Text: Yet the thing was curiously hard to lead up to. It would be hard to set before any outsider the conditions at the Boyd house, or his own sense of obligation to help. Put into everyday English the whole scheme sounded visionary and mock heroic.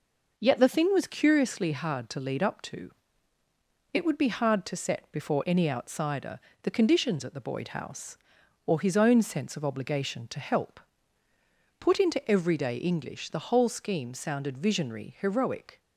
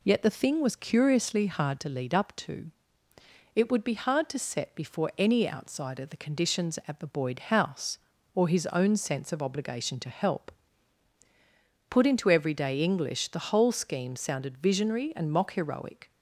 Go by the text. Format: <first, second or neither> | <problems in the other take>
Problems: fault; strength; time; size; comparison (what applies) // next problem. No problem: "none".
second | pauses between "outsider" and "the"; slight; at 6.3 s; 0.24 s long // skips "and mock"; at 15.1 s